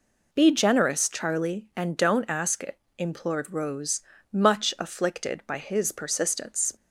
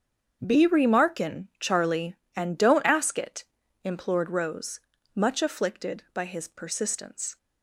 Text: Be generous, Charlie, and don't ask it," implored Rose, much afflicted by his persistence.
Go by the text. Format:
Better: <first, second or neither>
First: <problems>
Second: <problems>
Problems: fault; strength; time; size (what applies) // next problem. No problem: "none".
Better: first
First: none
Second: starts louder than the rest; strong; until 1.4 s; 7 dB // says "remarkin" for "generous"; at 0.6 s